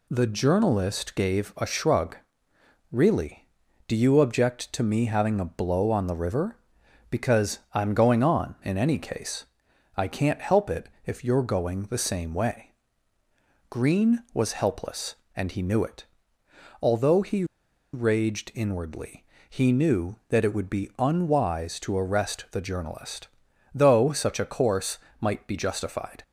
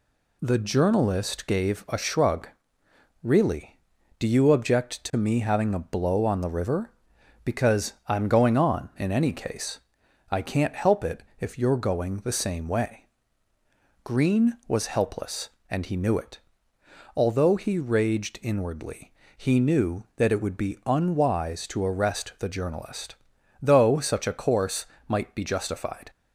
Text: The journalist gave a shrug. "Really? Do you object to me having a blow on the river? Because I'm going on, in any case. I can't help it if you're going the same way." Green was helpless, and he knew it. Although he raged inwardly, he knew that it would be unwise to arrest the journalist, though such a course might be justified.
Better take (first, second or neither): second